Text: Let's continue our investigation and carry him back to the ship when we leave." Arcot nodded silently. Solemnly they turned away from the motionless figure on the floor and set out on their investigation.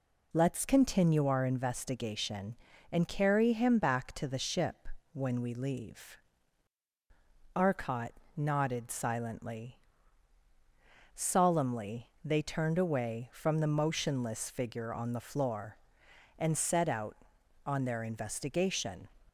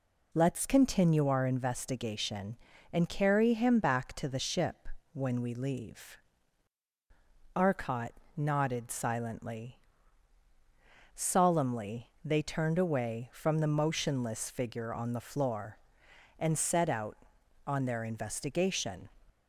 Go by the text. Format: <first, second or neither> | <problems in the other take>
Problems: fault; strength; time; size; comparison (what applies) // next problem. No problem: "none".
neither | pauses between "ship" and "when"; slight; the same in both // pauses between "Arcot" and "nodded"; slight; the same in both // pauses between "Solemnly" and "they"; slight; the same in both